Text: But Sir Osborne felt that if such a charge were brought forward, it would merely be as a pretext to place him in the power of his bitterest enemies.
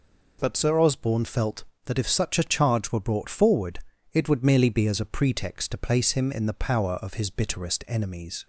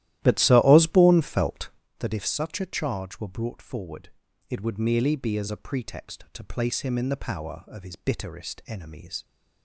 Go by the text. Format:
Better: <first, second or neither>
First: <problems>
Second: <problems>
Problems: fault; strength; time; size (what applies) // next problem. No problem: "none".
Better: first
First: none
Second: starts louder than the rest; strong; until 2.0 s; 14 dB